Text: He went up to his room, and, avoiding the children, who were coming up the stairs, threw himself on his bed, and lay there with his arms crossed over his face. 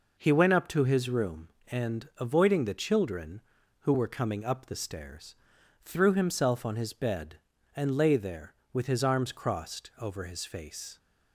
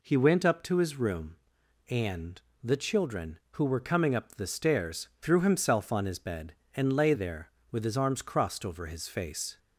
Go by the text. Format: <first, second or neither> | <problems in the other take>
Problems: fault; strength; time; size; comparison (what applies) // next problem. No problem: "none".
first | skips "avoiding"; at 2.5 s